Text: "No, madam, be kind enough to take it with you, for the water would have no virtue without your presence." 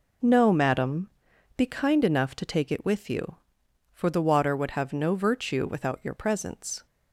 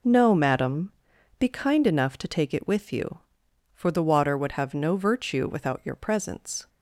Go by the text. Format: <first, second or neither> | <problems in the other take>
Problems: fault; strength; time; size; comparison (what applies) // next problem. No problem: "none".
neither | none